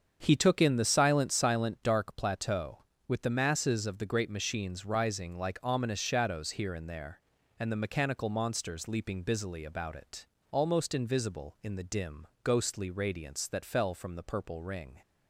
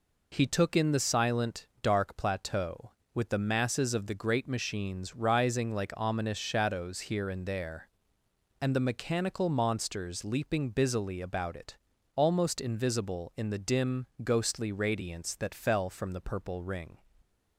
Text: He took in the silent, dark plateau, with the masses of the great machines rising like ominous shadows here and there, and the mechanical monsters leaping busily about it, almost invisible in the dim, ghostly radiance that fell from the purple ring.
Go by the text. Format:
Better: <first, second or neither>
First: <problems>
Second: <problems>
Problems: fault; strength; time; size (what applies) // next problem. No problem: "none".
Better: second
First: starts louder than the rest; strong; until 1.2 s; 7.5 dB // says "silent" twice; at 1.3 s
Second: none